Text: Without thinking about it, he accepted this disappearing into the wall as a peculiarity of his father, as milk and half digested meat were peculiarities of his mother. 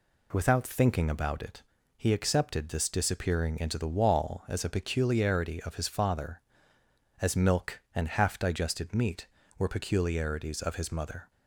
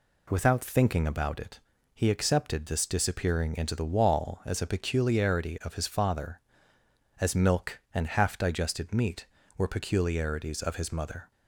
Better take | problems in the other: neither | none

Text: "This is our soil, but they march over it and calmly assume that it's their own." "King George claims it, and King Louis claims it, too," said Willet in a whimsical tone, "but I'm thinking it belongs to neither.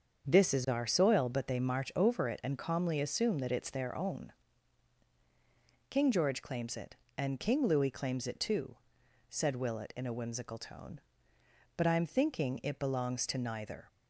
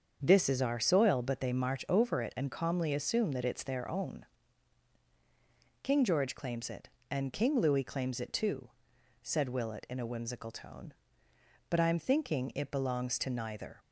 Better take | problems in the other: neither | starts louder than the rest; the same in both

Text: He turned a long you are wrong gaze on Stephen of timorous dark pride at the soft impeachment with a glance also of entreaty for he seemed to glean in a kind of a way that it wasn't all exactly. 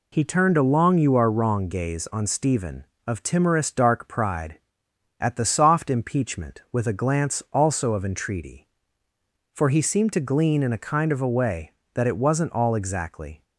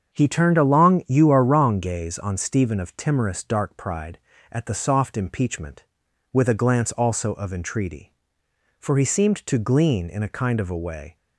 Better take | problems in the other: first | starts louder than the rest; strong; until 1.1 s; 7 dB // stops before "that it wasn't all exactly"; at 11.1 s

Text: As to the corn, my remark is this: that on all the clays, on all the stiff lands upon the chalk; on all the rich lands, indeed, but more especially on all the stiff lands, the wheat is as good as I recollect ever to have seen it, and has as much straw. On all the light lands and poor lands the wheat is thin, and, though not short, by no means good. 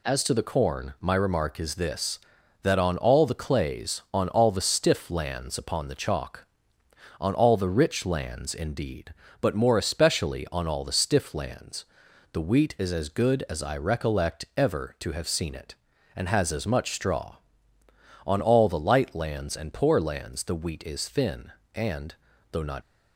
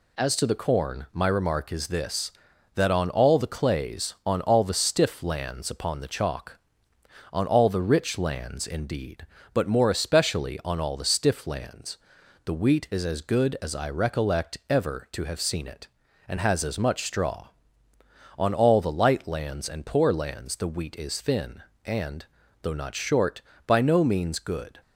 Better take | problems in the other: second | stops before "short by no means good"; at 22.8 s

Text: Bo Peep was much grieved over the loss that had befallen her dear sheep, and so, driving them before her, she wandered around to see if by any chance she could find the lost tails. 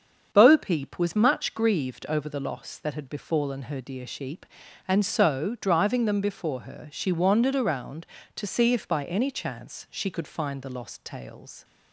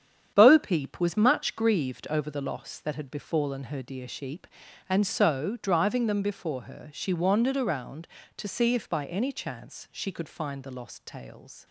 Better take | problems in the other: first | gets quieter; strong; throughout; 7.5 dB // starts louder than the rest; strong; until 1.3 s; 8.5 dB; strong in the first

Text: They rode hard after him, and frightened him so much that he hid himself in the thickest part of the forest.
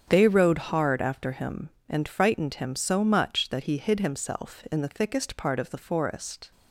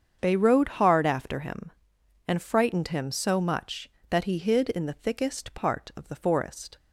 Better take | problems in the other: first | starts louder than the rest; strong; until 1.2 s; 7.5 dB; strong in the first // skips "himself"; at 4.6 s

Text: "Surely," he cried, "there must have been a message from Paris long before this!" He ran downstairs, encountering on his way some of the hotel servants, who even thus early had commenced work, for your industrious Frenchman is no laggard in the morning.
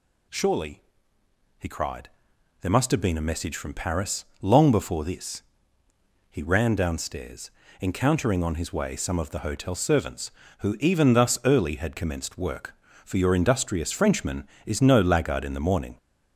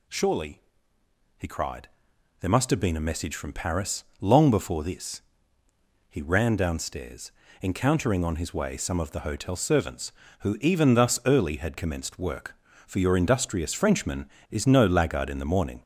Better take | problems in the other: neither | pauses between "Paris" and "long"; slight; the same in both

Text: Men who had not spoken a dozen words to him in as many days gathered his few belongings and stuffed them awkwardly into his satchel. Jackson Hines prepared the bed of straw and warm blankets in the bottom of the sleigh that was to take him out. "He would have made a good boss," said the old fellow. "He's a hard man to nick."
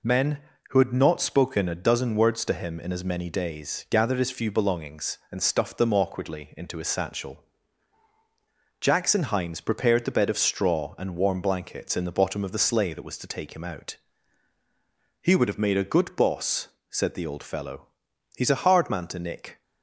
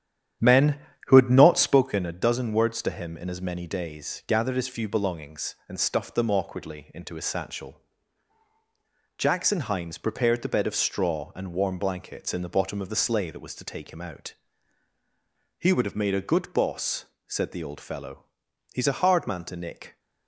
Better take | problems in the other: first | starts louder than the rest; strong; until 1.9 s; 10 dB

